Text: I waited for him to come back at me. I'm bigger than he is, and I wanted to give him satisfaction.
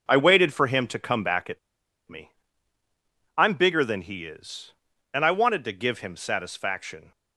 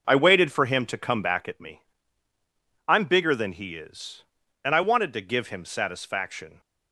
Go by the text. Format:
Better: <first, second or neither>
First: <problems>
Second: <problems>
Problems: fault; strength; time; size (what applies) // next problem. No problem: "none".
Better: second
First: pauses between "at" and "me"; noticeable; at 1.5 s; 0.50 s long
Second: none